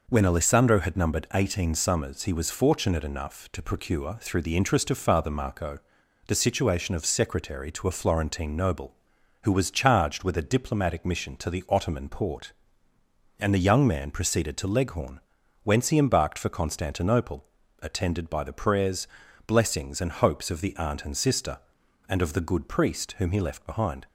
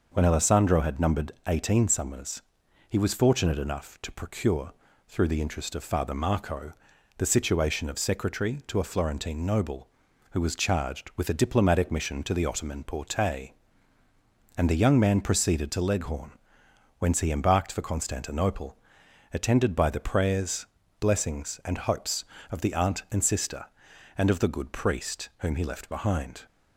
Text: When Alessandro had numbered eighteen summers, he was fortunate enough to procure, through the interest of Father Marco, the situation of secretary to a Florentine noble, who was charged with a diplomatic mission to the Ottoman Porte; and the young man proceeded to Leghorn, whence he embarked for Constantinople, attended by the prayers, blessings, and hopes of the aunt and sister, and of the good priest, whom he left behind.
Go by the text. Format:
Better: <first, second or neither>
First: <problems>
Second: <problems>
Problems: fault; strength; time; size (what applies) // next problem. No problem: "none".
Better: neither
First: none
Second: none